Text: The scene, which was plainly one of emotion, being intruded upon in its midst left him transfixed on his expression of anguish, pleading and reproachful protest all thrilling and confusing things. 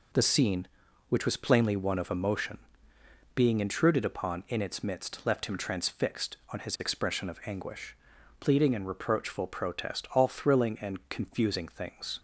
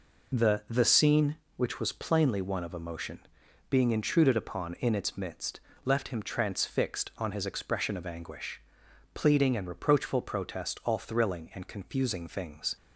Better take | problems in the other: first | says "The" twice; at 0.6 s // pauses between "midst" and "left"; slight; at 5.5 s; 0.26 s long

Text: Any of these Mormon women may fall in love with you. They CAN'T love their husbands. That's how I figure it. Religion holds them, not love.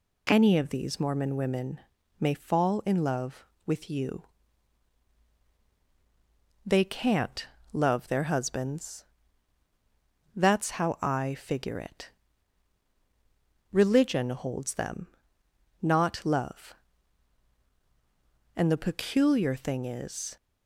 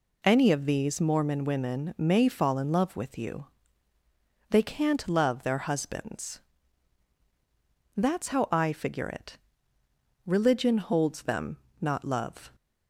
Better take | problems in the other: second | pauses between "women" and "may"; at 1.8 s; 0.40 s long // pauses between "CAN'T" and "love"; slight; at 7.4 s; 0.24 s long // goes on to say "And the peculiar thing is"; strong; from 18.5 s on; 1.8 s long

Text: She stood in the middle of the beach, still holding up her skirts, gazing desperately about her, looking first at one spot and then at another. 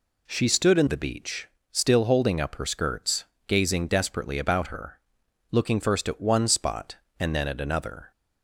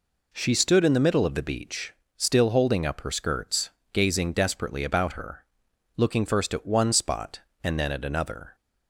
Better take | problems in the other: second | skips "the middle of"; at 0.8 s

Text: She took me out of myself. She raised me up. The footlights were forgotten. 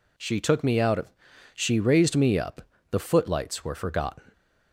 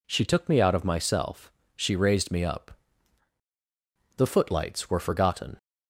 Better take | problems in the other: second | skips "myself"; at 1.3 s

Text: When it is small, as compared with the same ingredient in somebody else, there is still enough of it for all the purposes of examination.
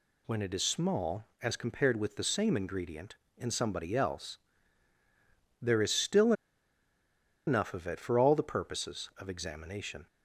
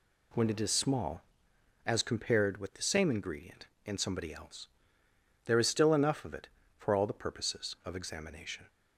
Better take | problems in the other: second | pauses between "still" and "enough"; at 6.3 s; 1.1 s long

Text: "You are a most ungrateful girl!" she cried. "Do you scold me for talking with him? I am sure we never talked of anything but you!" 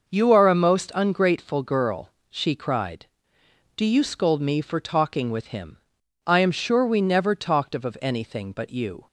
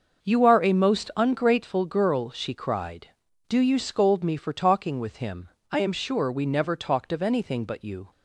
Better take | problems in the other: second | starts louder than the rest; noticeable; until 1.1 s; 6 dB; also in the second // says "of" twice; at 7.8 s

